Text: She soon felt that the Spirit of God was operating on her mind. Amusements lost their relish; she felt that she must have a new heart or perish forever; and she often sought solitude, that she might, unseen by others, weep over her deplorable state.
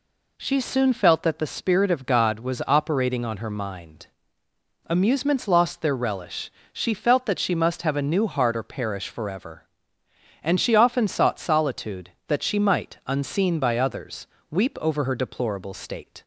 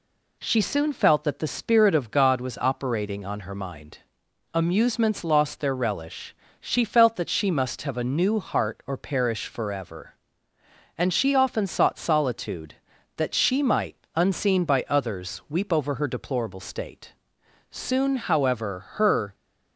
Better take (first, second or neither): first